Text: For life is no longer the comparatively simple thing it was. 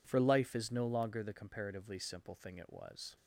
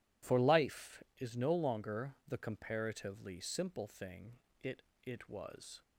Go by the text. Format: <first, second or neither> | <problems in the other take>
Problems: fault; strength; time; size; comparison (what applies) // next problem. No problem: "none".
first | pauses between "thing" and "it"; slight; at 4.3 s; 0.26 s long // says "it" twice; at 5.0 s